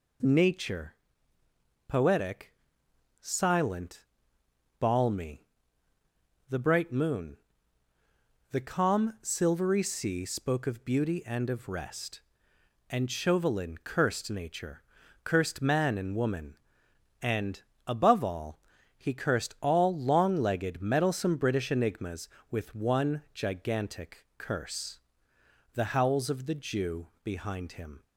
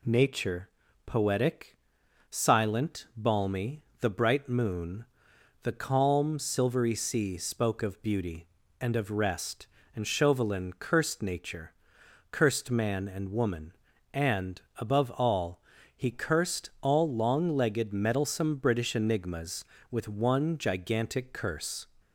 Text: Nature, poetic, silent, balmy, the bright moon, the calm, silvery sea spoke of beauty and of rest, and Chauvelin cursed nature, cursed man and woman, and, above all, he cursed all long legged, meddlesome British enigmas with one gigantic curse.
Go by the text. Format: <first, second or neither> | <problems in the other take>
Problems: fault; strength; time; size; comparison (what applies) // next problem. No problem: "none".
second | goes on to say "The howls of the Jew behind him"; strong; from 25.7 s on; 2.3 s long